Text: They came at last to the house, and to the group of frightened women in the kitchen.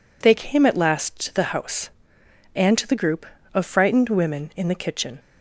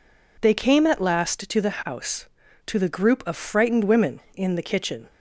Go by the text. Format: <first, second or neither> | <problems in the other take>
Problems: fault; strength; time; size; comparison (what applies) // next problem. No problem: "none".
first | skips "and"; at 2.4 s